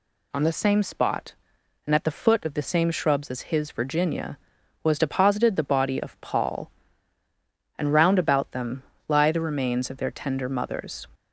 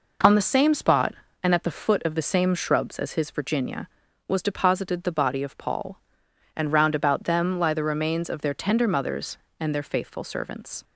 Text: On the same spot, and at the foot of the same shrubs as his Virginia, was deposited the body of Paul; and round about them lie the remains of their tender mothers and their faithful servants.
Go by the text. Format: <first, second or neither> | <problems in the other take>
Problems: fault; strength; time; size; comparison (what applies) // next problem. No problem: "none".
second | pauses between "them" and "lie"; slight; at 8.8 s; 0.24 s long // stops before "and their faithful servants"; at 11.1 s